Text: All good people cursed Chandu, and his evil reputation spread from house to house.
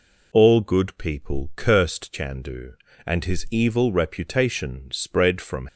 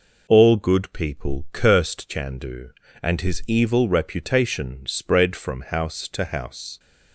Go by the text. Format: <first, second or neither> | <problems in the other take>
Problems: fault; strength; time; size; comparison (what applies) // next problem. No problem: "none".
second | stops before "house to house"; at 5.6 s